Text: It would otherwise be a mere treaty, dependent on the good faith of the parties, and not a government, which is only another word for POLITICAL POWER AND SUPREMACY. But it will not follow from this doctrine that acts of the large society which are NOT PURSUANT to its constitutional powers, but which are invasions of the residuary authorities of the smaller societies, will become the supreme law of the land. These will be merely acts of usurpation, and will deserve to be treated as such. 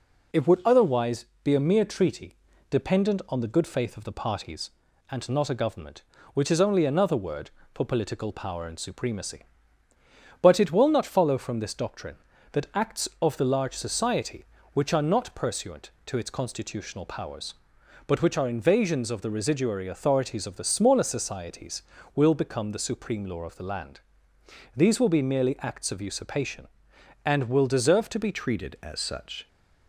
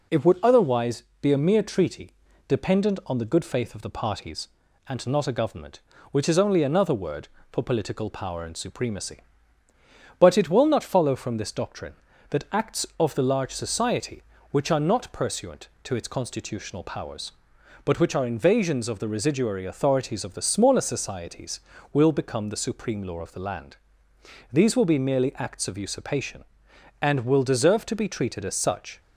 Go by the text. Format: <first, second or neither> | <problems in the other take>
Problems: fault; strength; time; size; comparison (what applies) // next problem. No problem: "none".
second | pauses between "otherwise" and "be"; slight; at 1.2 s; 0.18 s long; slight in the second // changes voice at "treated"; from 28.3 s on; 1.1 s long